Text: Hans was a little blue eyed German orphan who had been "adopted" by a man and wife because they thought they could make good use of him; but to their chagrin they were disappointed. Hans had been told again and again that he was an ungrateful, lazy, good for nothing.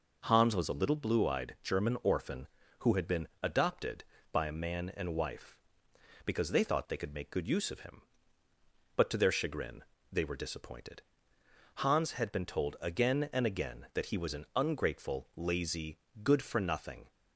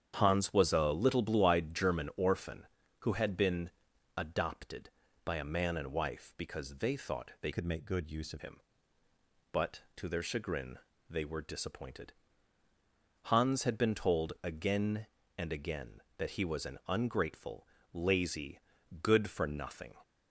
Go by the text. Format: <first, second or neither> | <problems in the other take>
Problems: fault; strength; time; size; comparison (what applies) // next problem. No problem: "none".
first | starts louder than the rest; strong; until 1.1 s; 8.5 dB // pauses between "been" and "adopted"; noticeable; at 3.7 s; 0.46 s long // changes voice from "could" to "of"; from 7.5 to 8.4 s; 0.9 s long // pauses between "chagrin" and "they"; slight; at 10.7 s; 0.30 s long; slight in the first